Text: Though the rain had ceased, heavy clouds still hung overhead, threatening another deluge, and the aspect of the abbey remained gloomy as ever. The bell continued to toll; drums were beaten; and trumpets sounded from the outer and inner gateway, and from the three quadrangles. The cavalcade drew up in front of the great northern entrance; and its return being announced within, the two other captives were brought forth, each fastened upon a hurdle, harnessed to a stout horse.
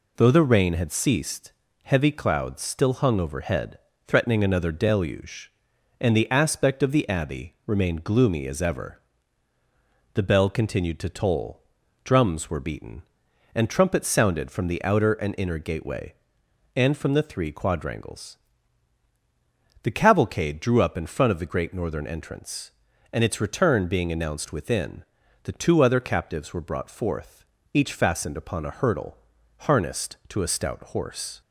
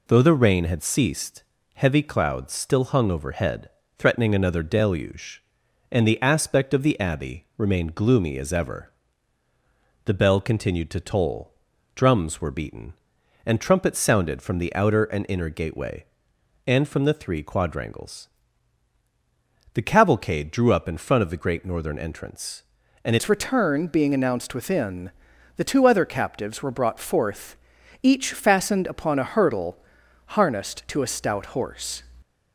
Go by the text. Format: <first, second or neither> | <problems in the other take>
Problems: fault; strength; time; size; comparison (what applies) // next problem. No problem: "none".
first | changes voice at "its"; from 23.1 s on; 8.9 s long